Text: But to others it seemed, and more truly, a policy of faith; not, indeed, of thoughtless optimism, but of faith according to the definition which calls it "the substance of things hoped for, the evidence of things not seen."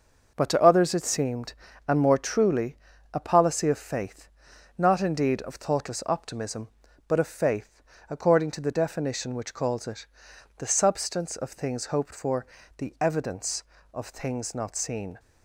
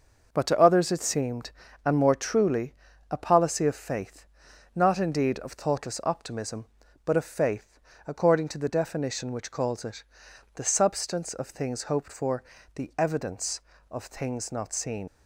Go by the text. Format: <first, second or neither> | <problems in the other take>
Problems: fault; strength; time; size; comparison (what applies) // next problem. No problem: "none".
first | pauses between "faith" and "according"; slight; at 7.7 s; 0.28 s long; slight in the first // pauses between "it" and "the"; noticeable; at 10.0 s; 0.54 s long; noticeable in the first // leaves "seen" unfinished; at 15.0 s; 85 ms